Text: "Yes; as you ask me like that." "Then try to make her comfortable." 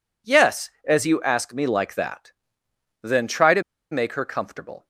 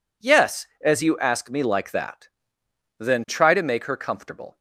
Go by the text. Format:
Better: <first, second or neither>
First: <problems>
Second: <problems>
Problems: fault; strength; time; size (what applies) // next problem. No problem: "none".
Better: second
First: pauses between "to" and "make"; slight; at 3.6 s; 0.29 s long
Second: none